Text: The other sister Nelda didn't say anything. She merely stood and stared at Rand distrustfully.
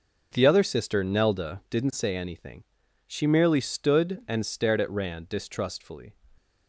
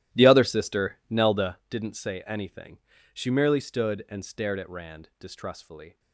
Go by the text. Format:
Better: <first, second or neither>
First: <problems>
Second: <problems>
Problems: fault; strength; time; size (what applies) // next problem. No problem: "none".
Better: first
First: none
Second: starts louder than the rest; strong; until 1.6 s; 13.5 dB